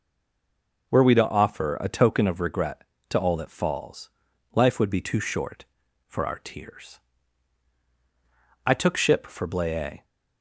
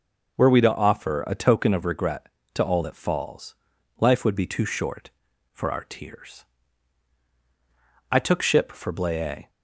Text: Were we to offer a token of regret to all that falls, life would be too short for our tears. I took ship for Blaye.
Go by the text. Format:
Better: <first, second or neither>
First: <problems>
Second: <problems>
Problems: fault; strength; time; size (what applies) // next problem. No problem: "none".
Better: second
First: stays silent before the first word; slight; until 0.8 s; 0.8 s long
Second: none